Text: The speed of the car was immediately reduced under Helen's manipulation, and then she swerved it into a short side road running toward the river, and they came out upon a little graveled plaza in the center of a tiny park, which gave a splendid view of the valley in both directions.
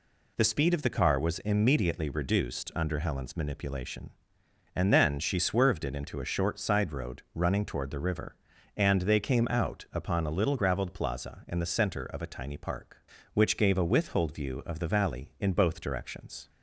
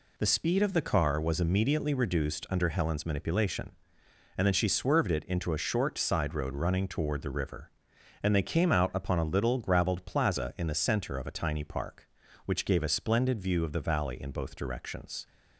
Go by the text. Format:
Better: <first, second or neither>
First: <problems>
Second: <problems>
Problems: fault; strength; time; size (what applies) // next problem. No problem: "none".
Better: second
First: says "withhold" for "splendid"; at 13.8 s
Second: none